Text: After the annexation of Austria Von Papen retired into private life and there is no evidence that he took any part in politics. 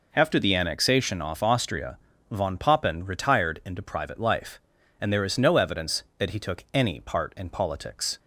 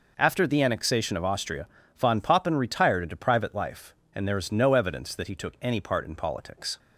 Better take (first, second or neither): second